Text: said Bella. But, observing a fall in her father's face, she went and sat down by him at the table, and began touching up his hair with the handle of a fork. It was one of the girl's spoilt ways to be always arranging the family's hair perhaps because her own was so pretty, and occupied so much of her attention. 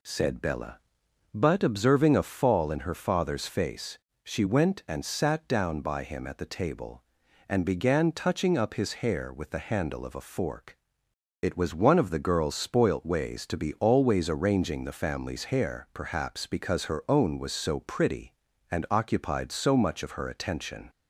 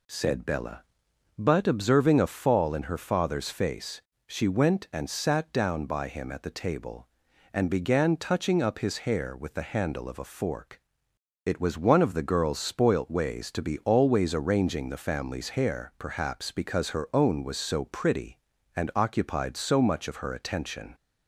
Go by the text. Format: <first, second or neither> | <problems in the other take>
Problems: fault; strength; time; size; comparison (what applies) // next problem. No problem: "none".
neither | none